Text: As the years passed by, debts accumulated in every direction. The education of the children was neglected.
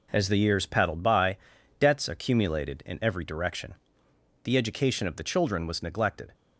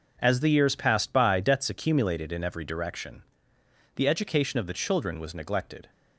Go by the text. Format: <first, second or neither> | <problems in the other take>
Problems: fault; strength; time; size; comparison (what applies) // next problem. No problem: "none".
second | says "paddled" for "passed"; at 0.6 s